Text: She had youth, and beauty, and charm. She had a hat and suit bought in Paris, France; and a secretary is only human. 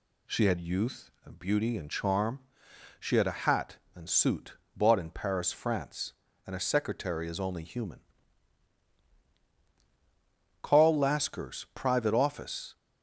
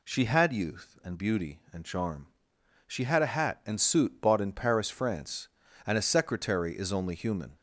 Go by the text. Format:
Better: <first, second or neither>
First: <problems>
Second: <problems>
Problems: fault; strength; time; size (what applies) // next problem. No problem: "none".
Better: second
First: pauses between "suit" and "bought"; slight; at 4.5 s; 0.18 s long // goes on to say "Carl Lasker's private office"; strong; from 10.6 s on; 2.1 s long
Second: none